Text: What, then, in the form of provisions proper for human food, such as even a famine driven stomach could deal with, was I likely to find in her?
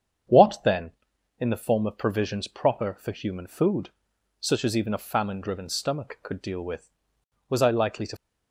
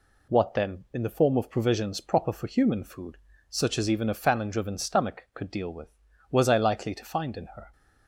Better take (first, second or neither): second